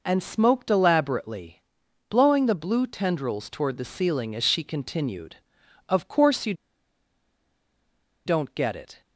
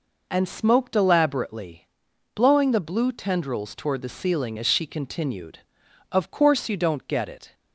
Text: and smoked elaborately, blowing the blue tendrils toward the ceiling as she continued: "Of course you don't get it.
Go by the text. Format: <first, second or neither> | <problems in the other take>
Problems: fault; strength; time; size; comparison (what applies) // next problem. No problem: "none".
second | pauses between "you" and "don't"; strong; at 6.5 s; 1.7 s long